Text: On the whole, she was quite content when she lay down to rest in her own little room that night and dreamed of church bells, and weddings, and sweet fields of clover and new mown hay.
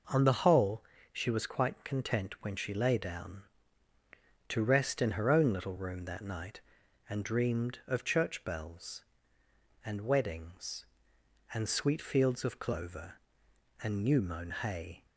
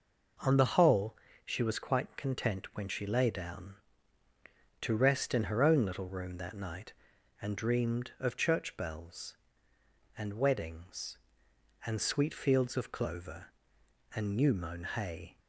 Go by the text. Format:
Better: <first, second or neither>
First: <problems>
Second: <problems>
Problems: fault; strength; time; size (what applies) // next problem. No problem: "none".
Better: neither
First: none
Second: none